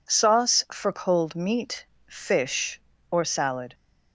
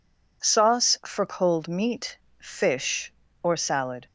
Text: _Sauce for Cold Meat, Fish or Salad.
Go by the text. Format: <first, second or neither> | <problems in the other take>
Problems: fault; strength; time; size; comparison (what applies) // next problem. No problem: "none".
neither | none